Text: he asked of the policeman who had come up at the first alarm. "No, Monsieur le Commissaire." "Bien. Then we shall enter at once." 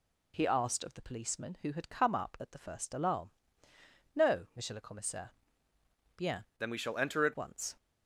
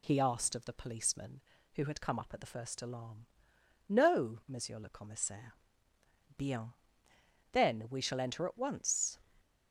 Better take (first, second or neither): second